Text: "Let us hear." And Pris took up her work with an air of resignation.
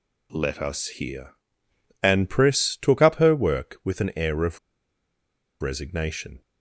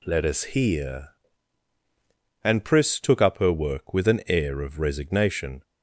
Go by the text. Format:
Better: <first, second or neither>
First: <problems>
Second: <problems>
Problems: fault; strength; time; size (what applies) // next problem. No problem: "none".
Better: second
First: pauses between "of" and "resignation"; at 4.5 s; 1.0 s long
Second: none